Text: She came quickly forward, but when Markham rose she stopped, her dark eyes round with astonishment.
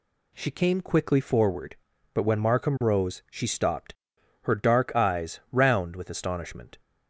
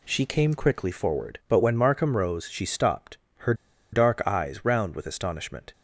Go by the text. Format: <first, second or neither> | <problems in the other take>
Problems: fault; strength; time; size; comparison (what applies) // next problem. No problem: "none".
first | pauses between "her" and "dark"; at 3.5 s; 0.38 s long